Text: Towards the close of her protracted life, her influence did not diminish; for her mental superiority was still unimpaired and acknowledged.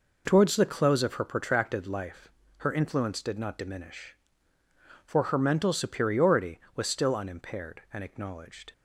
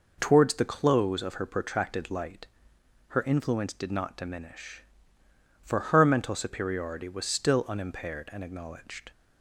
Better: first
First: none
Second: says "light" for "life"; at 2.1 s

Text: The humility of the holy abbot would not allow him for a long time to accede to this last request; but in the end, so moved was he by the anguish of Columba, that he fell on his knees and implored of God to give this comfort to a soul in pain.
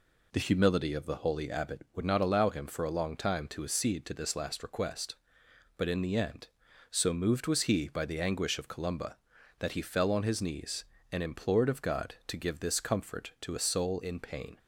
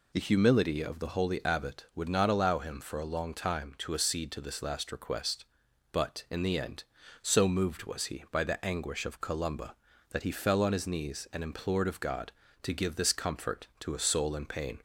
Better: neither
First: none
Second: none

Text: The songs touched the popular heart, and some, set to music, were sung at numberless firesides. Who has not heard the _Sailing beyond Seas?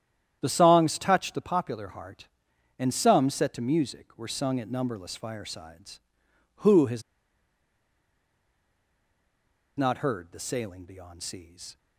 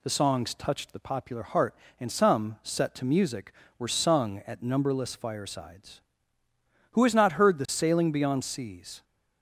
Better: second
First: starts louder than the rest; strong; until 1.4 s; 10 dB // pauses between "has" and "not"; strong; at 7.0 s; 2.7 s long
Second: none

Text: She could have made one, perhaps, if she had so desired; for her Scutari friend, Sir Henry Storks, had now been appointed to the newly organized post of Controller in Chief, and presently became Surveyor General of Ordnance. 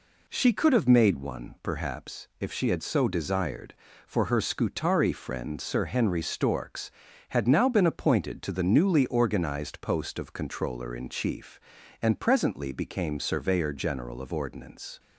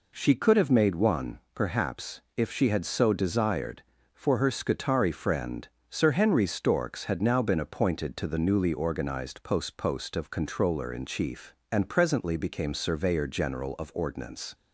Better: first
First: none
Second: says "post" twice; at 9.7 s

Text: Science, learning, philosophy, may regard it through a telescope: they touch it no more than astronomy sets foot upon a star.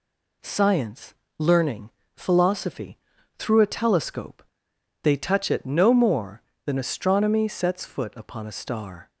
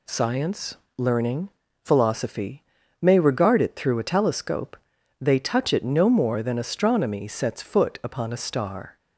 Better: second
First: skips "may regard it"; at 3.1 s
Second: none

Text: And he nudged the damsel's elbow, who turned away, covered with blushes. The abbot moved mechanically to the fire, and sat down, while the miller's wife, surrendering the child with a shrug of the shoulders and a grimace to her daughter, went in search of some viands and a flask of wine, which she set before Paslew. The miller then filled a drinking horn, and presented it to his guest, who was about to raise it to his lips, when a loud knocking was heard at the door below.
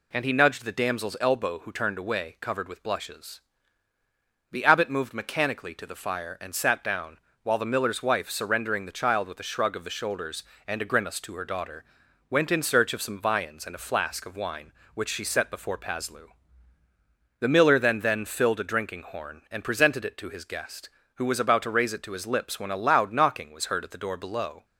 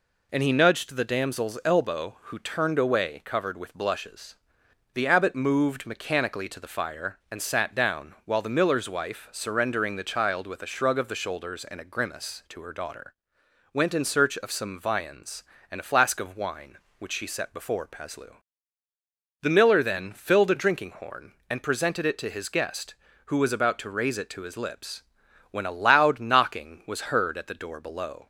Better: second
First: says "then" twice; at 17.9 s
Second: none

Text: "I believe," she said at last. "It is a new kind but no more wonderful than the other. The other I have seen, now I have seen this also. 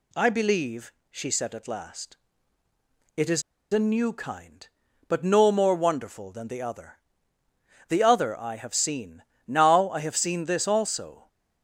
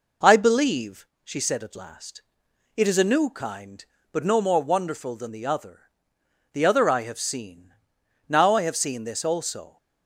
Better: second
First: pauses between "is" and "a"; slight; at 3.4 s; 0.29 s long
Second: none

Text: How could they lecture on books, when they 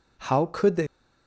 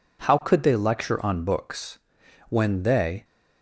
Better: second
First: stops before "lecture on books when they"; at 0.8 s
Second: none

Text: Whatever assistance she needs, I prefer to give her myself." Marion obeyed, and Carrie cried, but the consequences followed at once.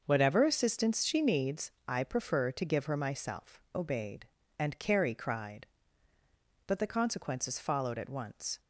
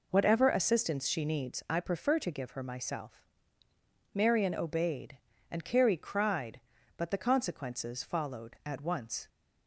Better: second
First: starts louder than the rest; until 1.0 s; 6 dB // skips "Marion"; at 3.6 s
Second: none

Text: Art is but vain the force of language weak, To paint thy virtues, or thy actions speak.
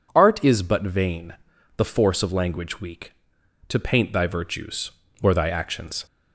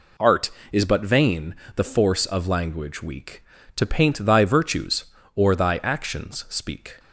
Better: second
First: pauses between "vain" and "the"; at 1.3 s; 0.44 s long // stops before "speak"; at 6.0 s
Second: pauses between "vain" and "the"; slight; at 1.5 s; 0.20 s long

